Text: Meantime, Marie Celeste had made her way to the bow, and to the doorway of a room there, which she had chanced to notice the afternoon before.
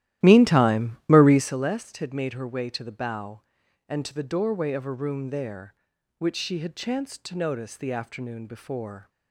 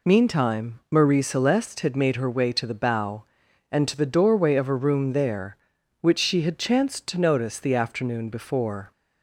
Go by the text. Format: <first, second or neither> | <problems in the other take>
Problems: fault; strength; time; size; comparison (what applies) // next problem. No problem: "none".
second | starts louder than the rest; strong; until 1.6 s; 13.5 dB